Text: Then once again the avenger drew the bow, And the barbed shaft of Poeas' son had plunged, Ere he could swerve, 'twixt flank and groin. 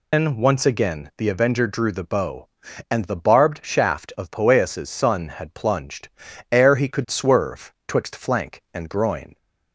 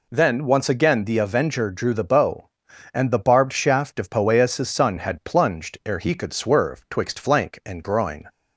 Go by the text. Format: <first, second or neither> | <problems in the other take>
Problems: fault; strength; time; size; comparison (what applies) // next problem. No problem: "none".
second | loses the start of "Then"; at 0.1 s; 165 ms